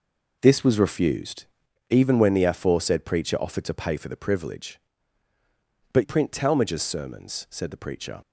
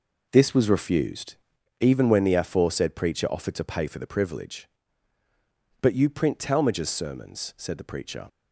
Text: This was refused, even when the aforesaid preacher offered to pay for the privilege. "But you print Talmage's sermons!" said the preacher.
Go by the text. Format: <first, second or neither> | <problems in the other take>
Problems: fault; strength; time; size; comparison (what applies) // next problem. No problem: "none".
second | skips "you"; at 6.0 s